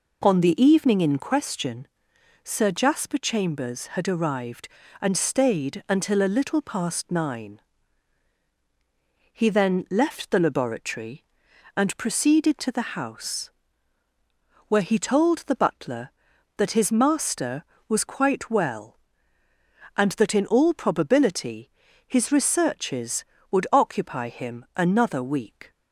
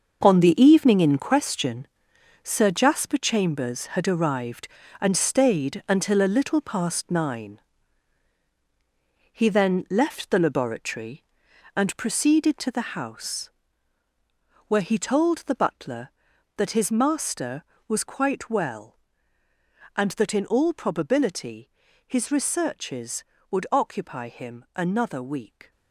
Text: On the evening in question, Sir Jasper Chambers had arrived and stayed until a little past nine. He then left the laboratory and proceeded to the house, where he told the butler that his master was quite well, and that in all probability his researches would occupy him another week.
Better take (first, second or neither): first